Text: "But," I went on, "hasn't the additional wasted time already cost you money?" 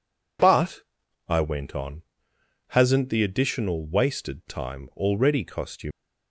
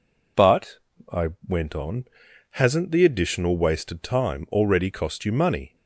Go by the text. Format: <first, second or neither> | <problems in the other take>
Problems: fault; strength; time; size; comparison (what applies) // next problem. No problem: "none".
second | stops before "money"; at 5.9 s